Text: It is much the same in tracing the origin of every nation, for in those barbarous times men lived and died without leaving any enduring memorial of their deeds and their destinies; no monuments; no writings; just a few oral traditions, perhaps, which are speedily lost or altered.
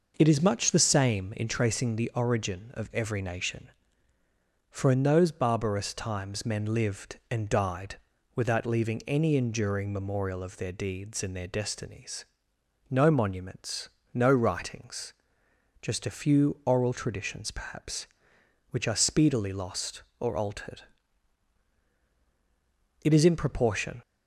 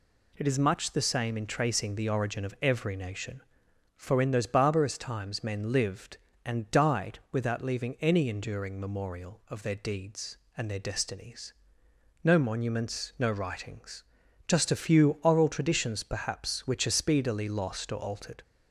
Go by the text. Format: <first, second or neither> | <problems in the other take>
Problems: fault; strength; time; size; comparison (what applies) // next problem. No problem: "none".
second | pauses between "died" and "without"; slight; at 7.9 s; 0.36 s long // goes on to say "It is in proportion"; noticeable; from 23.0 s on; 0.98 s long